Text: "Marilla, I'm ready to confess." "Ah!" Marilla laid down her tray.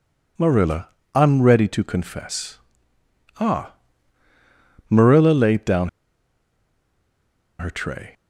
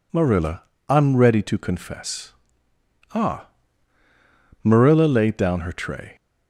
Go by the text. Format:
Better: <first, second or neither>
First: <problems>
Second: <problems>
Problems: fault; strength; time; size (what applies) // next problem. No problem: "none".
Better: second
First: pauses between "down" and "her"; strong; at 5.8 s; 1.7 s long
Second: none